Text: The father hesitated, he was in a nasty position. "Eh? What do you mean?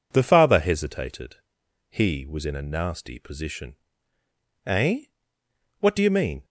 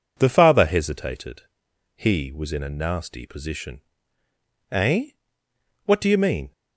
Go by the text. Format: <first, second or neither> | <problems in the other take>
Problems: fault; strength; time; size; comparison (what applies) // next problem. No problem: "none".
neither | none